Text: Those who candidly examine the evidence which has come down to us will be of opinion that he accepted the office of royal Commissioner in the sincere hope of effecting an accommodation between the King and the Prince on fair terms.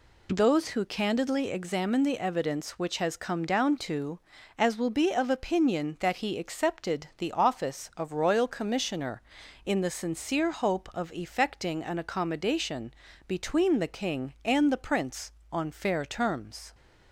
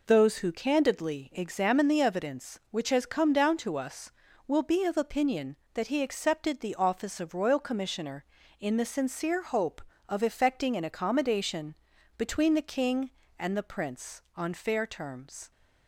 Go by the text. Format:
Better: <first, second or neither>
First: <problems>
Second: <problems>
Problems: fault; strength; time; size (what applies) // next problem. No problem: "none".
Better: second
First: says "as" for "us"; at 4.5 s // pauses between "accommodation" and "between"; slight; at 12.9 s; 0.32 s long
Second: pauses between "accommodation" and "between"; at 11.7 s; 0.40 s long